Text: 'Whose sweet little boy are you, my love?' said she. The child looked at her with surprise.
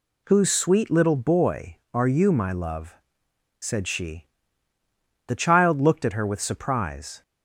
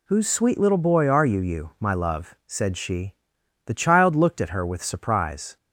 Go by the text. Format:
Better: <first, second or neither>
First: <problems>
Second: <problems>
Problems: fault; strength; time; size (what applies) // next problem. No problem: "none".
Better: first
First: none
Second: says "you" twice; at 1.4 s